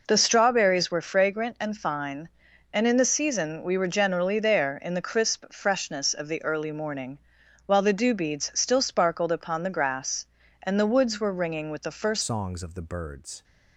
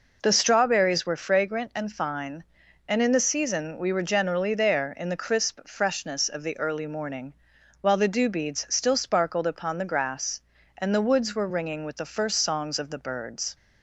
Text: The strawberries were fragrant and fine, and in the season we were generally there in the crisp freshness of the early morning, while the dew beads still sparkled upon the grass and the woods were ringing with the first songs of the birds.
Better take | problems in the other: second | changes voice at "songs"; from 12.2 s on; 1.2 s long

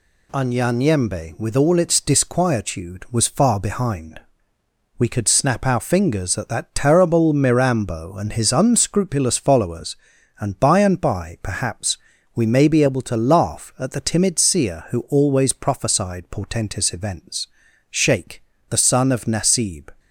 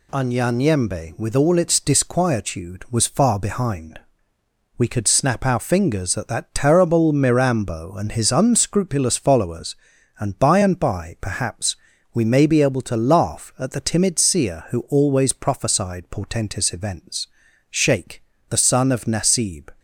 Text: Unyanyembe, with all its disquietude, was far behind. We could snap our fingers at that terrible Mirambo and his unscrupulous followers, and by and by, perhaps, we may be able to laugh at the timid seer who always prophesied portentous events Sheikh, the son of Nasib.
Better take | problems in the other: neither | pauses between "events" and "Sheikh"; the same in both

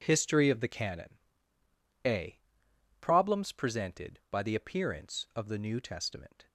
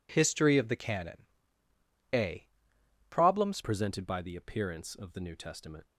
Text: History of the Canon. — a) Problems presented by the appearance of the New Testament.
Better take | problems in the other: first | changes voice at "presented"; from 3.6 s on; 2.2 s long

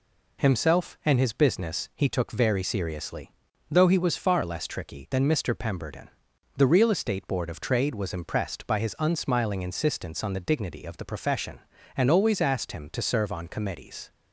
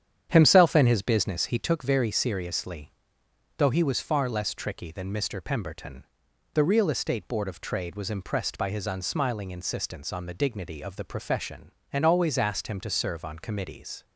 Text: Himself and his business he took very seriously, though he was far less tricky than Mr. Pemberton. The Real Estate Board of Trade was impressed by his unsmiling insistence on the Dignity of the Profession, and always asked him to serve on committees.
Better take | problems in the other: first | starts louder than the rest; strong; until 1.7 s; 9 dB

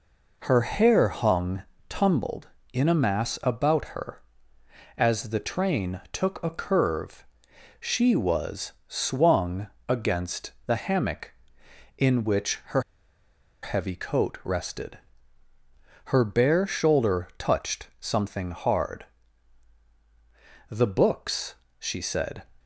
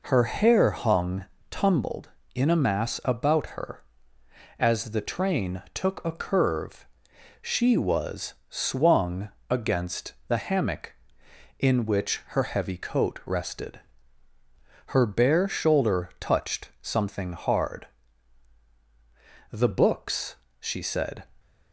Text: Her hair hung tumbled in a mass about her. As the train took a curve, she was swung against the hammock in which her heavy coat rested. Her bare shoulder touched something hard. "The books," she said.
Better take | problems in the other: second | pauses between "hung" and "tumbled"; slight; at 1.6 s; 0.24 s long; slight in the second // pauses between "swung" and "against"; slight; at 9.6 s; 0.20 s long; slight in the second // pauses between "her" and "heavy"; noticeable; at 12.8 s; 0.81 s long

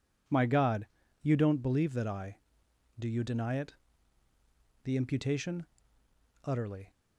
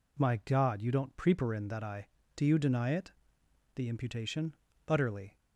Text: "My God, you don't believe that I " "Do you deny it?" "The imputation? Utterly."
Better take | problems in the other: first | says "preparin" for "believe"; at 1.1 s

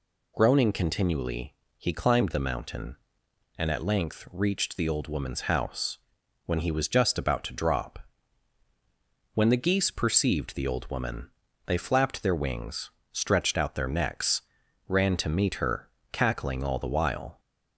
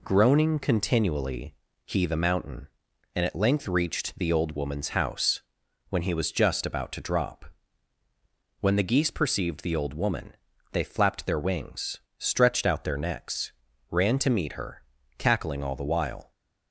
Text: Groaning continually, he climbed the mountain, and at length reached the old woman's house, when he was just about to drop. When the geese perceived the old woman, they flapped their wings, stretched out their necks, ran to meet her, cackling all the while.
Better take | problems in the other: first | skips "climbed"; at 2.0 s

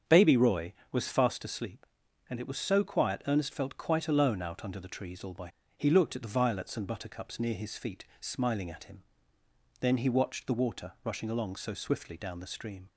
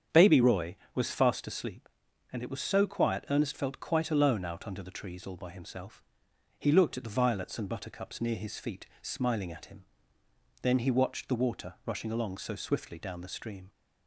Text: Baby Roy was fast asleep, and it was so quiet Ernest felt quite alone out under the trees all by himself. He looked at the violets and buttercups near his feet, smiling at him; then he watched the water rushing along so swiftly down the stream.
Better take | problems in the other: second | starts louder than the rest; strong; until 1.2 s; 7.5 dB; strong in the second // skips "himself"; at 5.6 s

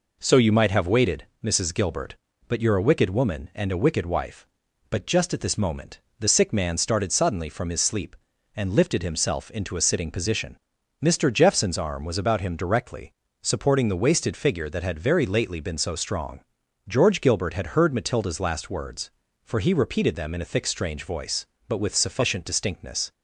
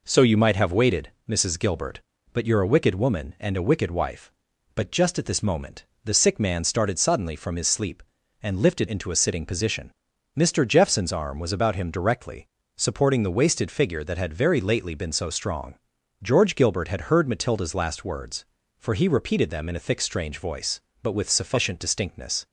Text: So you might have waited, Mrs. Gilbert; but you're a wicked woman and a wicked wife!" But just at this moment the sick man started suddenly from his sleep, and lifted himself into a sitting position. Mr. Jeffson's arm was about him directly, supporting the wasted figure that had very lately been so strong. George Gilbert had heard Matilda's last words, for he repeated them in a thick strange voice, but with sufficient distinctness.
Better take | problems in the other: first | pauses between "moment" and "the"; slight; at 5.8 s; 0.20 s long; slight in the first // skips "himself"; at 8.8 s

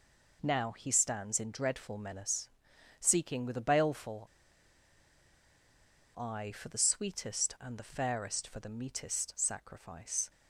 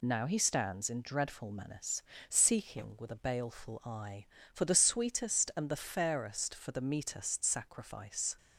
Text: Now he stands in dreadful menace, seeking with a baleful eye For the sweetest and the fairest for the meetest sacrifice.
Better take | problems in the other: second | pauses between "baleful" and "eye"; strong; at 4.2 s; 1.9 s long

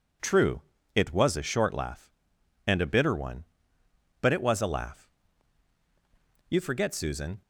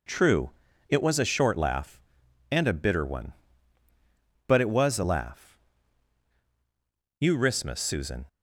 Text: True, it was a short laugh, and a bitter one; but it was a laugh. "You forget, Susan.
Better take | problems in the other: first | says "rismus" for "forget"; at 7.3 s

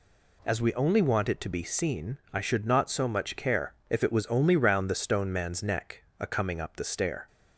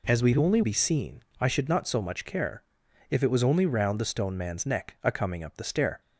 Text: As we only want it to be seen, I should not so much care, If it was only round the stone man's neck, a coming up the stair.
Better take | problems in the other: first | skips "want it to"; at 0.6 s

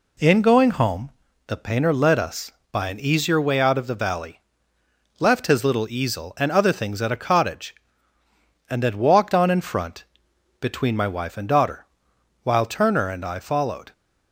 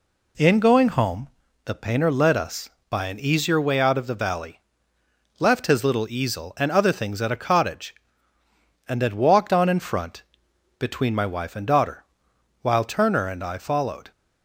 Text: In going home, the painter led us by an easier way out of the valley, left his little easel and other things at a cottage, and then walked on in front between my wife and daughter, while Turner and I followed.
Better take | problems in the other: neither | pauses between "front" and "between"; noticeable; the same in both

